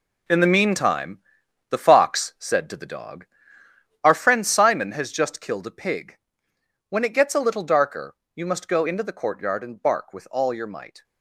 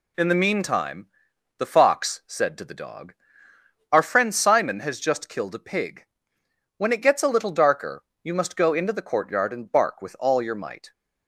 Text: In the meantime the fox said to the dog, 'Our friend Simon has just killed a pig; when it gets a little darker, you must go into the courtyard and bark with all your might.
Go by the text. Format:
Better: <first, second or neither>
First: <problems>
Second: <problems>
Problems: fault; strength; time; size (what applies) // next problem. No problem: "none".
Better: second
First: gets quieter; strong; throughout; 10 dB // pauses between "meantime" and "the"; noticeable; at 1.2 s; 0.50 s long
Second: pauses between "meantime" and "the"; noticeable; at 1.0 s; 0.50 s long